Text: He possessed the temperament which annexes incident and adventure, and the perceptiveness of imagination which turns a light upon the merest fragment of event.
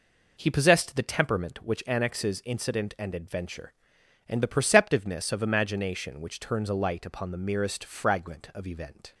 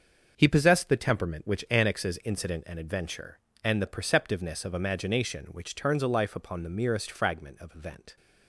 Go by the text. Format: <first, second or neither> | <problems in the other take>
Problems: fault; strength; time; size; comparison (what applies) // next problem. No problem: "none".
first | starts louder than the rest; until 1.3 s; 6.5 dB // says "life" for "light"; at 6.0 s